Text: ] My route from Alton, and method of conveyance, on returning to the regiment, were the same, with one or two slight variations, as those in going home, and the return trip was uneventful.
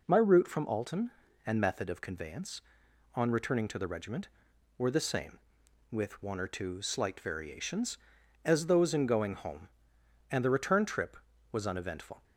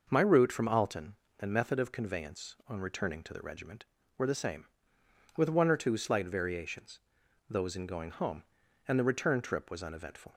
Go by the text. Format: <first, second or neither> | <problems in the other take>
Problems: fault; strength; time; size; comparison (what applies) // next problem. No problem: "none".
first | skips "as"; at 7.2 s